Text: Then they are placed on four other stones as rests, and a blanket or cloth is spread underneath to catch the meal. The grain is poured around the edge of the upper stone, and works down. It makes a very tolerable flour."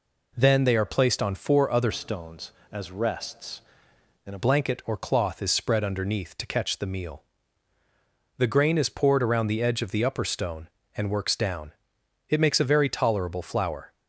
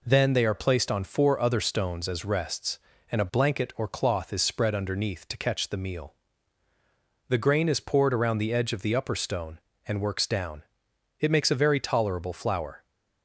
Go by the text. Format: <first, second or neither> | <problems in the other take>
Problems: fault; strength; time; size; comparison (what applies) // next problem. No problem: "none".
second | changes voice from "stones" to "a"; from 1.9 to 4.3 s; 2.4 s long